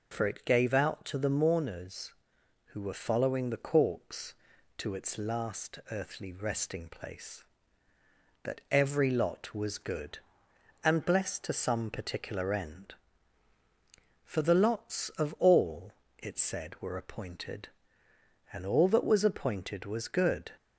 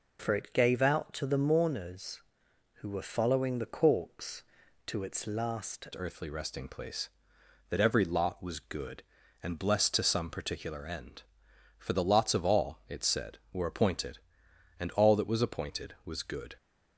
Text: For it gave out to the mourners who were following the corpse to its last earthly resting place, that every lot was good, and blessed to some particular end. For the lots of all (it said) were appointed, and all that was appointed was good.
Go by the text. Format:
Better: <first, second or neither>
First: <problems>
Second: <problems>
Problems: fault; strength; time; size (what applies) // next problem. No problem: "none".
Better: first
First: none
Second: changes voice at "earthly"; from 5.9 s on; 10.6 s long